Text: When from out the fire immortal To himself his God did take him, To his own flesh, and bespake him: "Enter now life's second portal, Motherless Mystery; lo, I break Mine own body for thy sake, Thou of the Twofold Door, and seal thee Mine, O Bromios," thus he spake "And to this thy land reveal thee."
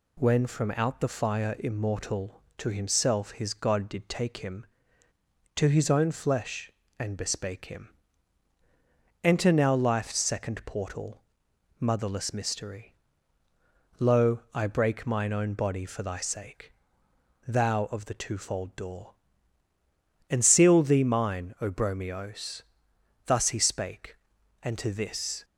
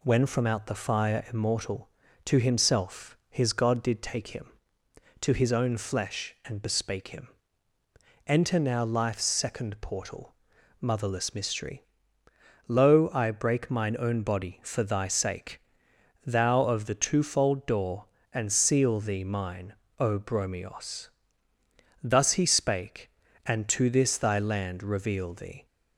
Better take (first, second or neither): second